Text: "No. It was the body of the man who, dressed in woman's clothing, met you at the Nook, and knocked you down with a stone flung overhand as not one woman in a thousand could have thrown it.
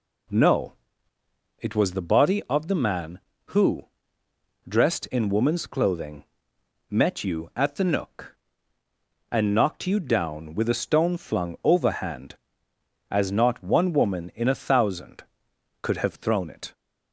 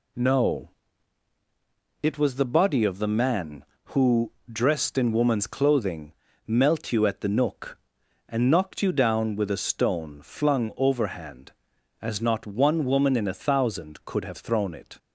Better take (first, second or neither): first